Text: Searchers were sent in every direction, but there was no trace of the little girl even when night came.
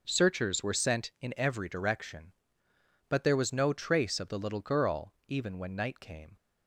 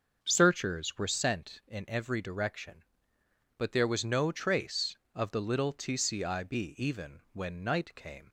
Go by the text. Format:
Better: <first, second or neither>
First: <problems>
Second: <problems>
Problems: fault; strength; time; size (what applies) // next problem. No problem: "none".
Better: first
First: none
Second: starts louder than the rest; until 1.2 s; 6 dB // says "tcib" for "girl"; at 5.7 s